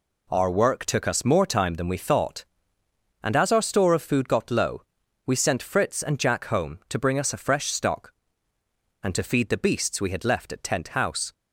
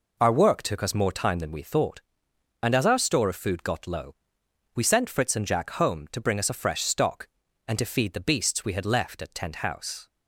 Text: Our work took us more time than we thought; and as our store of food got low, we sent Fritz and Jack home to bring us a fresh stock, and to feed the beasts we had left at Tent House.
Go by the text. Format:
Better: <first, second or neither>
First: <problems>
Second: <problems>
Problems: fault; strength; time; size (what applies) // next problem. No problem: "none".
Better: neither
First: none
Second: none